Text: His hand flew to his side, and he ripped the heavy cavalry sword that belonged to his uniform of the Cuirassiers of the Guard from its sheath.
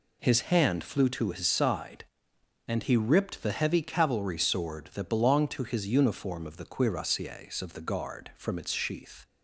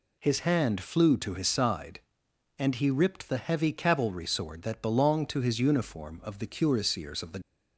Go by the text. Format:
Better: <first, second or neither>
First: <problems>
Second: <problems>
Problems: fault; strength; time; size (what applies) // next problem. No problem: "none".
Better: first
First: none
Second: stops before "Guard from its sheath"; at 7.4 s